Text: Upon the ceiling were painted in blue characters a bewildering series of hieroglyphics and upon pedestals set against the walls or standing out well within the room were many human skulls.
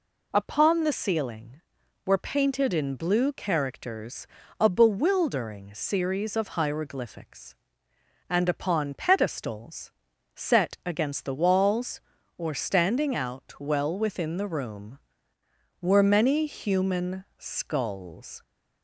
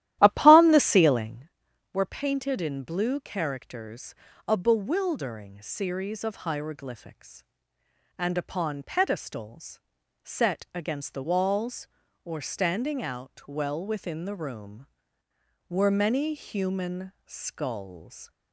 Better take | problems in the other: first | starts louder than the rest; strong; until 1.5 s; 13.5 dB // pauses between "characters" and "a"; slight; at 4.1 s; 0.34 s long; slight in the first // pauses between "pedestals" and "set"; at 9.8 s; 0.42 s long; also in the first

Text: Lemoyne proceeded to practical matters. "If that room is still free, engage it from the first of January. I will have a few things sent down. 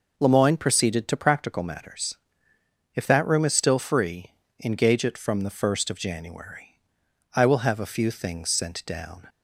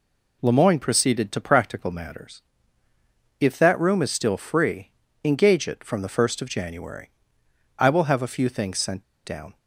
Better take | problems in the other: first | pauses between "sent" and "down"; slight; at 9.0 s; 0.21 s long

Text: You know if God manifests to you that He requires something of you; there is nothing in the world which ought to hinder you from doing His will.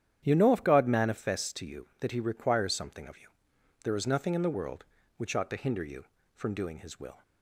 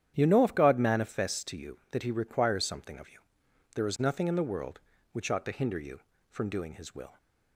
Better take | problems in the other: neither | starts louder than the rest; strong; the same in both

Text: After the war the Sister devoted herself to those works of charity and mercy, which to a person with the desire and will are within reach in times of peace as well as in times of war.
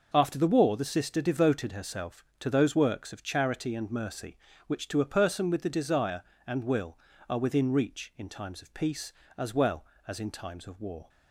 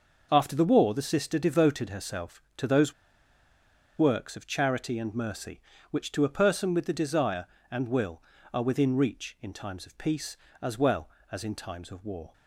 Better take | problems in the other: first | pauses between "those" and "works"; at 2.9 s; 1.0 s long

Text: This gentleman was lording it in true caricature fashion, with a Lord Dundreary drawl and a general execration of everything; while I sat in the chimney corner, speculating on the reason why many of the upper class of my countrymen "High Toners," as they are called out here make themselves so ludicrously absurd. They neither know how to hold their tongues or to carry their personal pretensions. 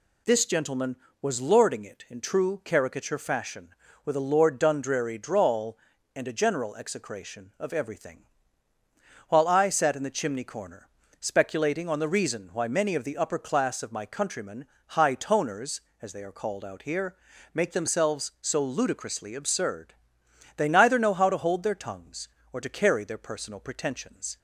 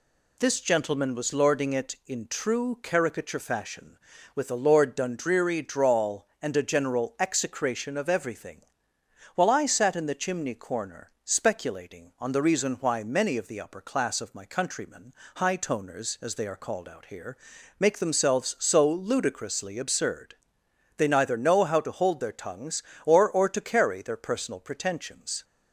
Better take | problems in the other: first | pauses between "countrymen" and "High"; slight; at 15.1 s; 0.24 s long; slight in the first // pauses between "here" and "make"; at 17.3 s; 0.40 s long; also in the first // says "or" twice; at 23.2 s

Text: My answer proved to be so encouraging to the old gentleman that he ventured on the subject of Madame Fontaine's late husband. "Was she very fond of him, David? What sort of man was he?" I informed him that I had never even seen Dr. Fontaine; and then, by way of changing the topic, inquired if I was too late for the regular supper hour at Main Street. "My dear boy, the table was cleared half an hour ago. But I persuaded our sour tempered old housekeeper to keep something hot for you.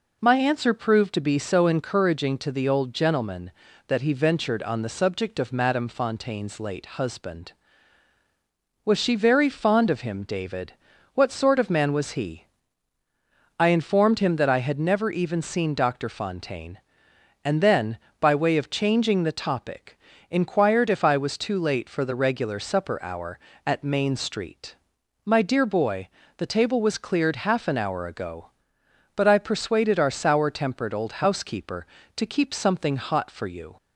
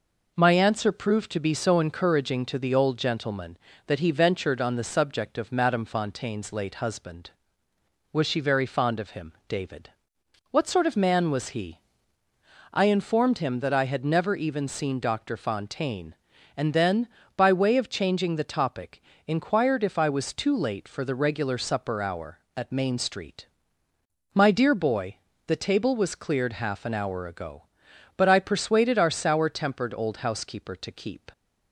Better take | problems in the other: first | stops before "something hot for you"; at 31.3 s

